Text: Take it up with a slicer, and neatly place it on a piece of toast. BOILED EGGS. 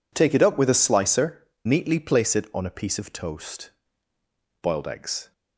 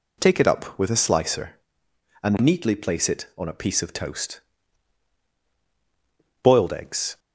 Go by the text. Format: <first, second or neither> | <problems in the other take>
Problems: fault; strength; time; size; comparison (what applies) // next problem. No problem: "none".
second | skips "and"; at 1.5 s